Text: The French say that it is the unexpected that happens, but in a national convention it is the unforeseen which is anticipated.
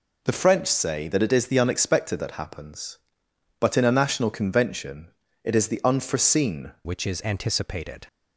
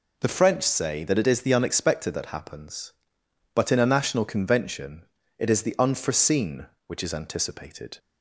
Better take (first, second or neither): second